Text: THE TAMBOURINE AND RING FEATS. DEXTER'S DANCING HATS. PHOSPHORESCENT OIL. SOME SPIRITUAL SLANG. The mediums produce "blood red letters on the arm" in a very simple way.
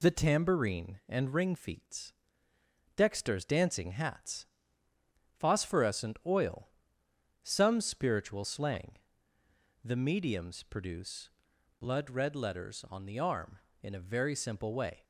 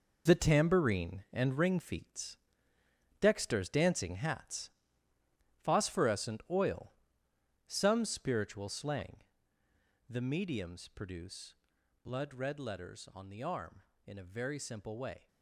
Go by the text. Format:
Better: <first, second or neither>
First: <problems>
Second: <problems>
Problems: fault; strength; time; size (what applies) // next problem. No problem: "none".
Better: first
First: pauses between "produce" and "blood"; noticeable; at 11.2 s; 0.50 s long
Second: gets quieter; strong; throughout; 10 dB // pauses between "produce" and "blood"; noticeable; at 11.5 s; 0.50 s long